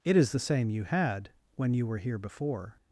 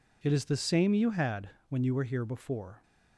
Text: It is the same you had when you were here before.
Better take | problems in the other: neither | pauses between "had" and "when"; slight; the same in both

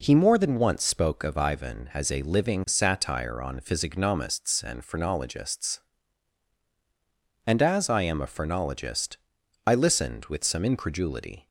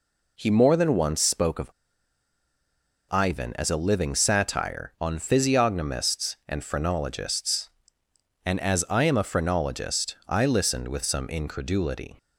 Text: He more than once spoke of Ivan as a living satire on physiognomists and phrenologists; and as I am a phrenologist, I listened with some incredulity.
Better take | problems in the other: first | pauses between "of" and "Ivan"; strong; at 1.7 s; 1.3 s long

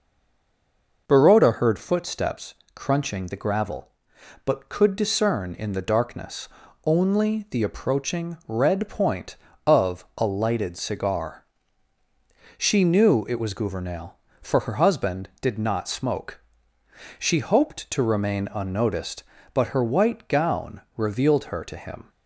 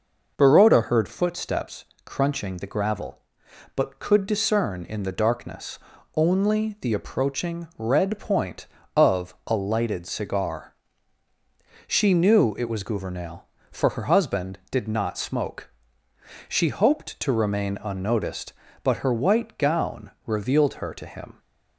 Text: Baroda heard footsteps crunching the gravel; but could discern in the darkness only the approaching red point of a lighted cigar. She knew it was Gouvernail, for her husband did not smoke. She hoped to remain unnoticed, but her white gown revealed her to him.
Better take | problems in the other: second | stays silent before the first word; until 1.0 s; 1.0 s long // pauses between "footsteps" and "crunching"; slight; at 2.5 s; 0.20 s long; slight in the second // pauses between "darkness" and "only"; slight; at 6.4 s; 0.36 s long; slight in the second // pauses between "gown" and "revealed"; slight; at 20.7 s; 0.16 s long; slight in the second

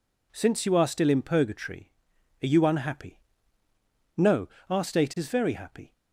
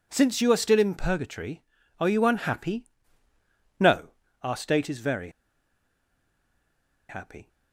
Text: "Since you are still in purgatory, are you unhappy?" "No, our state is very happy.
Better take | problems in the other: first | pauses between "very" and "happy"; strong; at 5.2 s; 1.8 s long

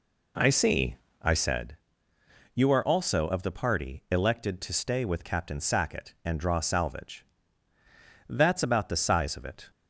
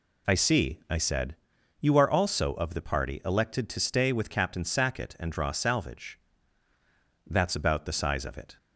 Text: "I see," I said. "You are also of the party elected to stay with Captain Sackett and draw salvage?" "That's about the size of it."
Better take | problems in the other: second | starts louder than the rest; slight; until 1.6 s; 3 dB

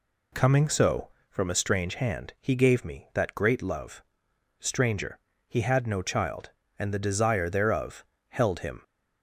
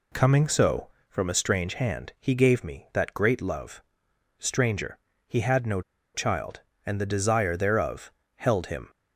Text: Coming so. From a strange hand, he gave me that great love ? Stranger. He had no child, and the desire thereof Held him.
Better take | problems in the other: first | pauses between "no" and "child"; slight; at 5.8 s; 0.33 s long // pauses between "thereof" and "Held"; slight; at 8.1 s; 0.24 s long; slight in the first

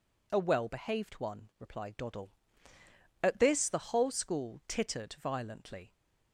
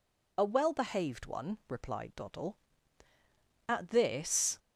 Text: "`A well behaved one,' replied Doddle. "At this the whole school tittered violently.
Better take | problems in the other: first | stops before "the whole school tittered violently"; at 4.5 s

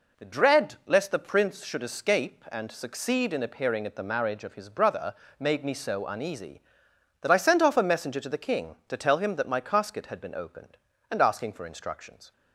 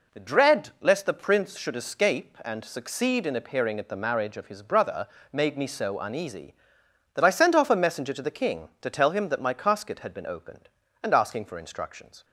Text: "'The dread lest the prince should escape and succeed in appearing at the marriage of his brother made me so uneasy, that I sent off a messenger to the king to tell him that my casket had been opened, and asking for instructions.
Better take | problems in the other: neither | pauses between "brother" and "made"; slight; the same in both

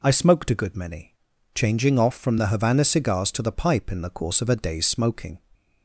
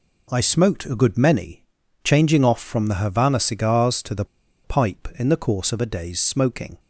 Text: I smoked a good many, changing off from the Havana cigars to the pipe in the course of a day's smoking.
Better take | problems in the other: first | pauses between "the" and "pipe"; at 4.2 s; 0.39 s long

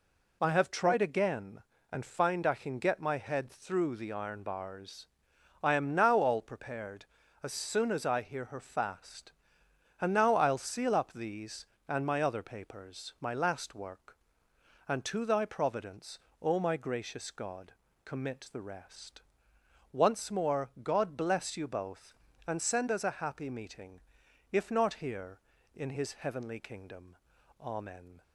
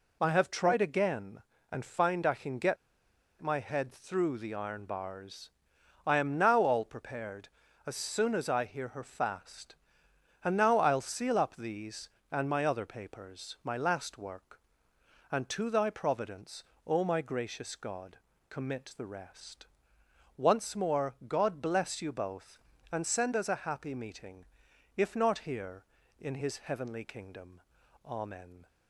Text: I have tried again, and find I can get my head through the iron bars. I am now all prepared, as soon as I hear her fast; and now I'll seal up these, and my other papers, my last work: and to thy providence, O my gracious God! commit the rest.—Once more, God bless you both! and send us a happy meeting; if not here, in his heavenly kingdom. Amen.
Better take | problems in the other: first | pauses between "get" and "my"; noticeable; at 2.7 s; 0.64 s long

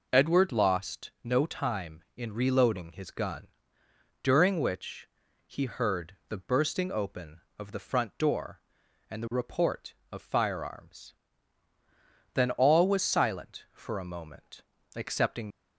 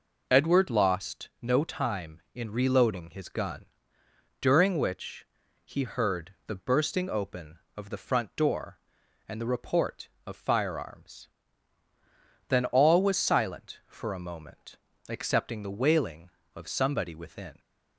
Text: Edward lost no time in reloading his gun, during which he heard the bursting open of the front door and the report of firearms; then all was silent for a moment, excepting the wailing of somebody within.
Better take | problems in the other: second | pauses between "which" and "he"; at 5.0 s; 0.38 s long; also in the second // stops before "the wailing of somebody within"; at 15.4 s

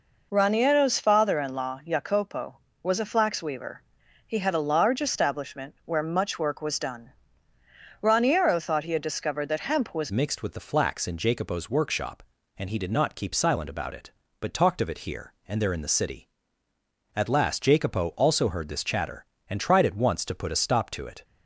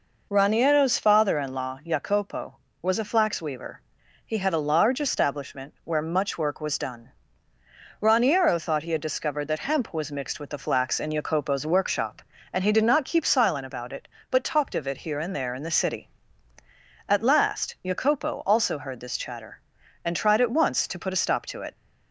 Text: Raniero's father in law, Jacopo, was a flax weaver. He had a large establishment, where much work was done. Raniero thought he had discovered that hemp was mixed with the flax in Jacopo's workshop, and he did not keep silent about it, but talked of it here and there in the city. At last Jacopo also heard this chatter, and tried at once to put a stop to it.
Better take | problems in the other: second | changes voice at "mixed"; from 10.0 s on; 11.2 s long

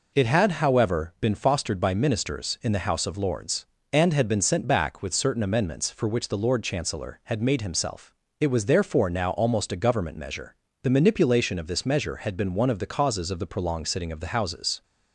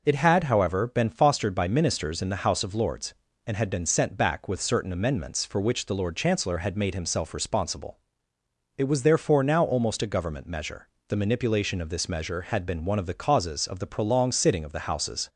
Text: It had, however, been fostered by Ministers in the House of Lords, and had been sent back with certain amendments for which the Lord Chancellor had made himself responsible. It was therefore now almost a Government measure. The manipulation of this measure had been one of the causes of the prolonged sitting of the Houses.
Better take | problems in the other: second | skips "responsible"; at 8.2 s

